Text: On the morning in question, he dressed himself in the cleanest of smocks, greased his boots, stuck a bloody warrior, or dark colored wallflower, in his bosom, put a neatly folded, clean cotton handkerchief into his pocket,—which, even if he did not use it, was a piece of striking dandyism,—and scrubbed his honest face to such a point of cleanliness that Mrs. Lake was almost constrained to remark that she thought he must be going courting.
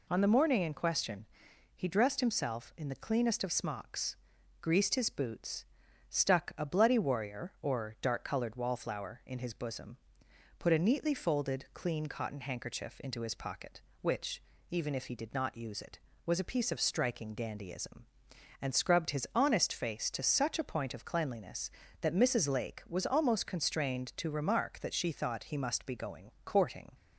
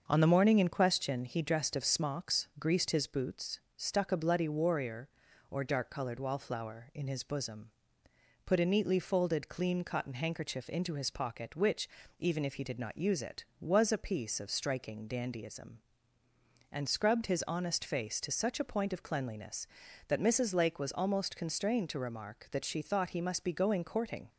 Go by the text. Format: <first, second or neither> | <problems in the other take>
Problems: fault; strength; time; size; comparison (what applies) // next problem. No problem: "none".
first | starts louder than the rest; until 1.0 s; 6.5 dB // skips "himself in the cleanest"; at 1.7 s